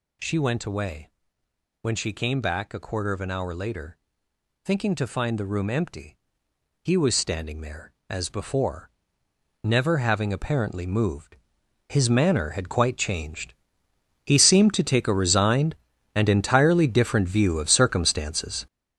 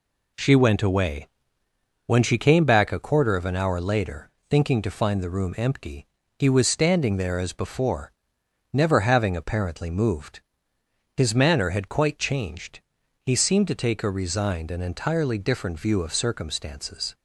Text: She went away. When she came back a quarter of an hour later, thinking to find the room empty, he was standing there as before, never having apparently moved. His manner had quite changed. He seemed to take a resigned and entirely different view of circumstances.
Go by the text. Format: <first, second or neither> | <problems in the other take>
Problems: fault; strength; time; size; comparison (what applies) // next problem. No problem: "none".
second | gets louder; strong; throughout; 8.5 dB